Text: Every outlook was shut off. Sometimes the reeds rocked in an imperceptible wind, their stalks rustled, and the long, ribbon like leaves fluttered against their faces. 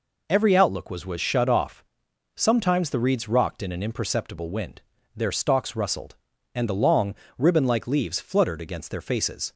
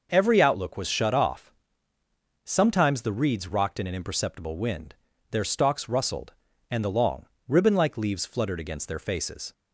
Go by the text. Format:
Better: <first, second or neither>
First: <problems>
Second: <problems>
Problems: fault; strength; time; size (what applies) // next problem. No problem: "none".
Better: second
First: says "was" twice; at 1.0 s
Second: none